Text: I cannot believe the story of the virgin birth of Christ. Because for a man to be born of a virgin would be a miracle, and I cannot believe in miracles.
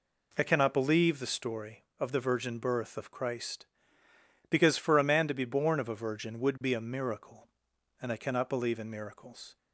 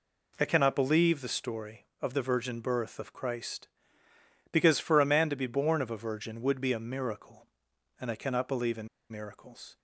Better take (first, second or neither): first